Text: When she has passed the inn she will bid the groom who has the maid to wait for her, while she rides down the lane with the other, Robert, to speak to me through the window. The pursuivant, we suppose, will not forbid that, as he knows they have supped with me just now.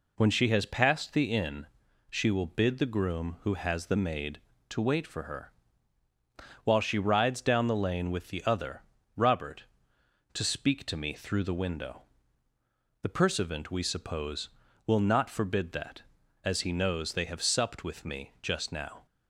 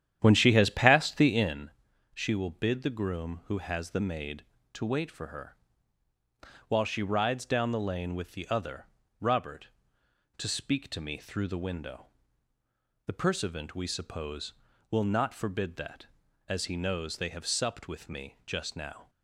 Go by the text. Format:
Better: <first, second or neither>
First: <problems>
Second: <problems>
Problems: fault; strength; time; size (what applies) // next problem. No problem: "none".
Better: first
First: pauses between "inn" and "she"; at 1.6 s; 0.42 s long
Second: starts louder than the rest; strong; until 1.7 s; 10 dB // pauses between "inn" and "she"; at 1.7 s; 0.42 s long